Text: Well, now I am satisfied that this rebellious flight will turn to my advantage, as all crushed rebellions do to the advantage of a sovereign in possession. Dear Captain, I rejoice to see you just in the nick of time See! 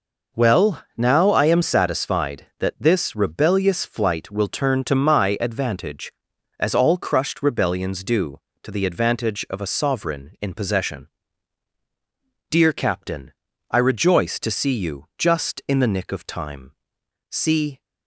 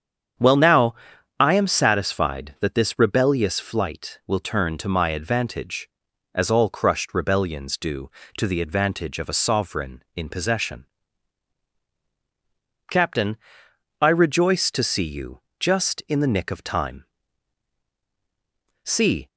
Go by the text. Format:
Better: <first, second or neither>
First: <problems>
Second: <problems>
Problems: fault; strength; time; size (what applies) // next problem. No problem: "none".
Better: first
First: pauses between "time" and "See"; noticeable; at 16.7 s; 0.58 s long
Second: starts louder than the rest; strong; until 1.8 s; 8 dB // pauses between "now" and "I"; at 0.9 s; 0.44 s long // skips "Dear"; at 11.8 s // pauses between "you" and "just"; slight; at 15.4 s; 0.18 s long // pauses between "time" and "See"; strong; at 17.0 s; 1.8 s long